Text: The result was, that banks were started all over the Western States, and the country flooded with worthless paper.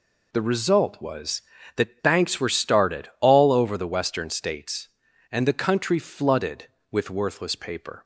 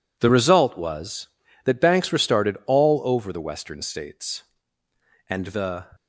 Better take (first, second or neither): first